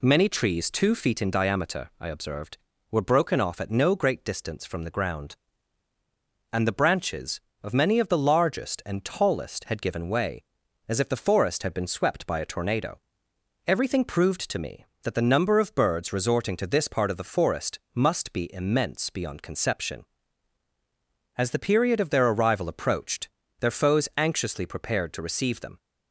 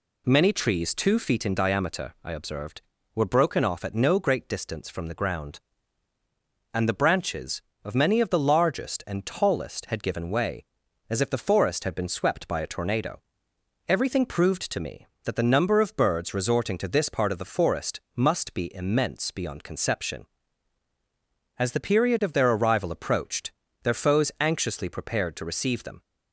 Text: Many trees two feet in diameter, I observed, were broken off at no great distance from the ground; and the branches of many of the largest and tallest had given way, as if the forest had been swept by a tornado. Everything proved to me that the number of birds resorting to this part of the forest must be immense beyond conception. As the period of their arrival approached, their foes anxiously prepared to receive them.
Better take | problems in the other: neither | none

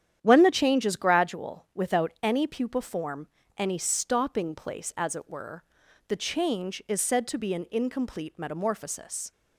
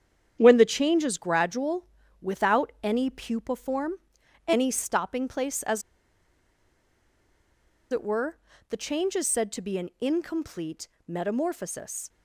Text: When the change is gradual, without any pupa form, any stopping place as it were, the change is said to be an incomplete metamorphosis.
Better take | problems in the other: first | starts louder than the rest; strong; until 1.4 s; 9 dB; strong in the first // pauses between "as" and "it"; strong; at 5.8 s; 2.1 s long // pauses between "incomplete" and "metamorphosis"; slight; at 10.8 s; 0.18 s long

